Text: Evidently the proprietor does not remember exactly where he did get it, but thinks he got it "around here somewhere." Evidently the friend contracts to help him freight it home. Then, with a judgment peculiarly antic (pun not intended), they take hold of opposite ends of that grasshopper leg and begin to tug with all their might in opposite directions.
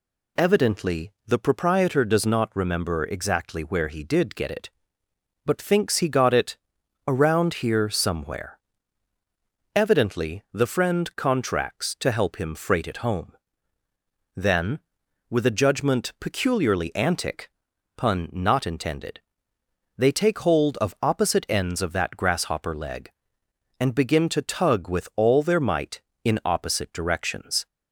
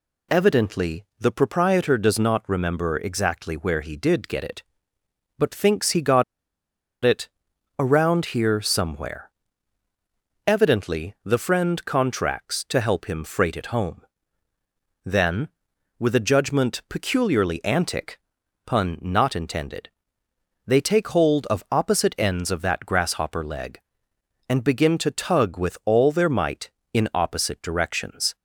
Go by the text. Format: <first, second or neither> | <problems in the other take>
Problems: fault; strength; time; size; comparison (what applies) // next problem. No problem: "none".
first | pauses between "got" and "it"; noticeable; at 6.2 s; 0.81 s long // pauses between "it" and "around"; noticeable; at 7.2 s; 0.50 s long; noticeable in the first